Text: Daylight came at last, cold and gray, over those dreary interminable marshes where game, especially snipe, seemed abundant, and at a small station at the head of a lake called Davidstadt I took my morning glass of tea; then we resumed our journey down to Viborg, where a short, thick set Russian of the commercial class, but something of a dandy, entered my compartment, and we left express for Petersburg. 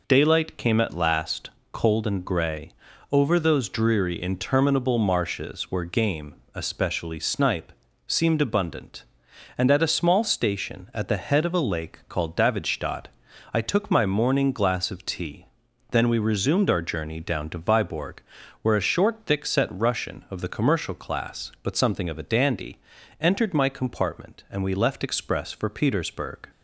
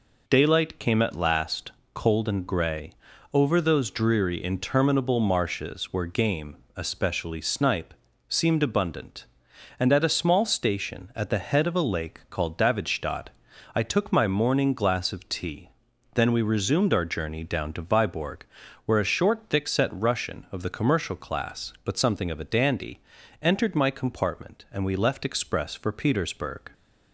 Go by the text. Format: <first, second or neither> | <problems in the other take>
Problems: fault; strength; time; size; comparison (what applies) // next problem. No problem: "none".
neither | pauses between "Davidstadt" and "I"; noticeable; the same in both